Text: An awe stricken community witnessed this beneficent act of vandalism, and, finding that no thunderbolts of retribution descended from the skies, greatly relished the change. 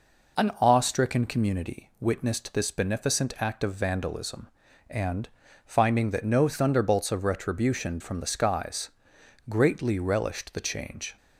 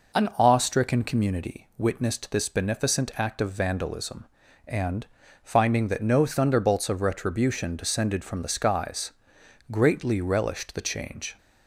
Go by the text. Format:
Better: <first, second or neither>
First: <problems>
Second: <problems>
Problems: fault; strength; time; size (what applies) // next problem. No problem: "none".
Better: second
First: skips "descended"; at 7.9 s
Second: none